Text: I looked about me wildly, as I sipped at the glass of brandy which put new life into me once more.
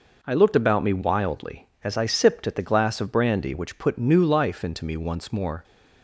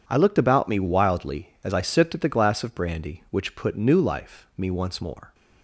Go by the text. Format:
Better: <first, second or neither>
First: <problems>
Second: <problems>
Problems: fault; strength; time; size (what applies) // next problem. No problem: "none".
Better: first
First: none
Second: skips "into"; at 4.5 s